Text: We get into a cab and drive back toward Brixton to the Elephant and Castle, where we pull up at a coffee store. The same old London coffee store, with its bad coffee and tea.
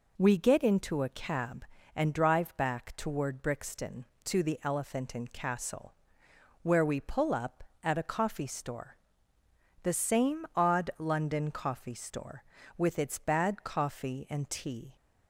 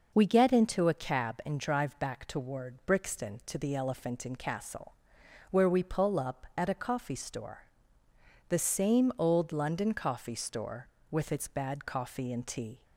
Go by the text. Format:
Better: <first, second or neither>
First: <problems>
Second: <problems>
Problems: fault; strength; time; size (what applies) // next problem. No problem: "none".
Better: second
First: says "odd" for "old"; at 10.5 s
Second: none